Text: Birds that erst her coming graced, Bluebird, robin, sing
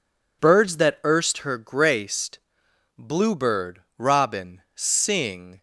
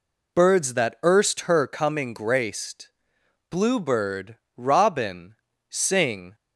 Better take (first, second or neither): second